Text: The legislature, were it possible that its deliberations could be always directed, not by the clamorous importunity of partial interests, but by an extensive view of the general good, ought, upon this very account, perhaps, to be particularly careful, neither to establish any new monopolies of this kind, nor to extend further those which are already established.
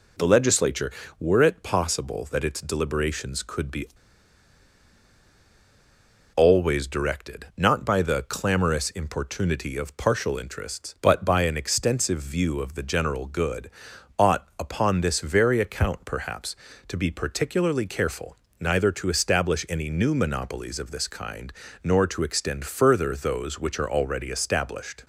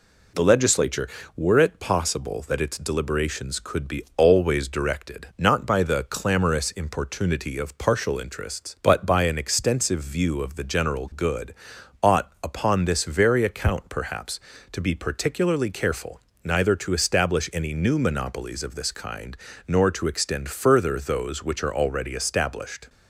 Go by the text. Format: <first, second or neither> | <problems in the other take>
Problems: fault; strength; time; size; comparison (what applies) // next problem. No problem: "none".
second | pauses between "be" and "always"; strong; at 3.8 s; 2.4 s long